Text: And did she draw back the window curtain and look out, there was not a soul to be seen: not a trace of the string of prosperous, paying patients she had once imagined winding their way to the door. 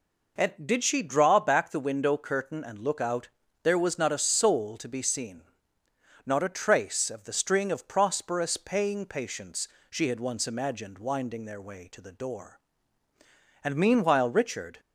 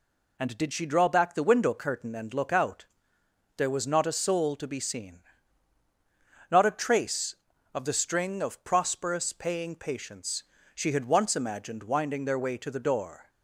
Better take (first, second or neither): second